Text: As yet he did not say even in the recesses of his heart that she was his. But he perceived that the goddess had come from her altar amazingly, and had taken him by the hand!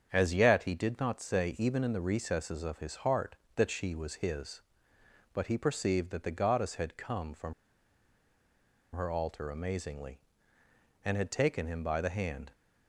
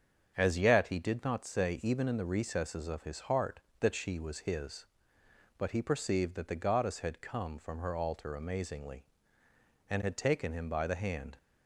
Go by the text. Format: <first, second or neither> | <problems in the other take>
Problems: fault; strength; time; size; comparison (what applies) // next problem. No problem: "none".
second | starts louder than the rest; strong; until 1.1 s; 7.5 dB; strong in the second // pauses between "from" and "her"; strong; at 7.5 s; 1.4 s long